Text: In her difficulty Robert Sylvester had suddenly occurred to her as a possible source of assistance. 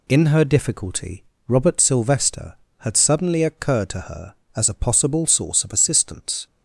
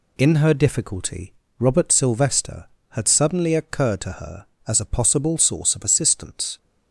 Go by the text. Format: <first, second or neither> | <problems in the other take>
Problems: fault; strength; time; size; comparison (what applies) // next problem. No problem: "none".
neither | pauses between "difficulty" and "Robert"; slight; the same in both